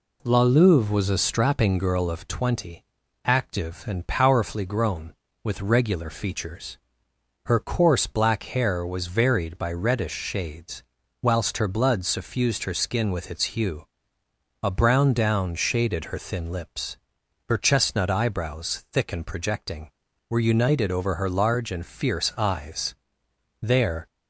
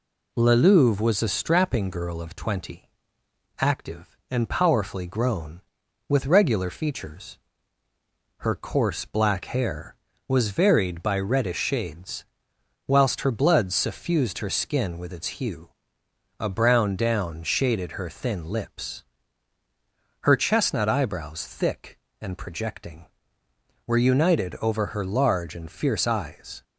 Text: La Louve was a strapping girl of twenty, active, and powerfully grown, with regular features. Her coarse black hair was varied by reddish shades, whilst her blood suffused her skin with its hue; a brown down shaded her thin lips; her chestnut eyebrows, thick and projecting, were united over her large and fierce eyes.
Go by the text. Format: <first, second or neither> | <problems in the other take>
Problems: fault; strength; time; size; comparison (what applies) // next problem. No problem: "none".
second | goes on to say "There"; slight; from 23.6 s on; 0.44 s long